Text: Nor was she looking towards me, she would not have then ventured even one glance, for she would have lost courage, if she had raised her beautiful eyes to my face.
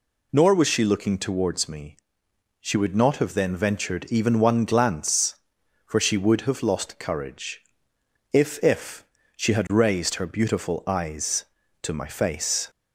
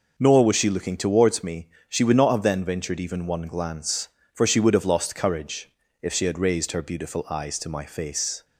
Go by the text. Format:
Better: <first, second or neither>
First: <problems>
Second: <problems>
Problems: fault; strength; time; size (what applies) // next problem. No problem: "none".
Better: second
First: says "if" twice; at 8.6 s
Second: none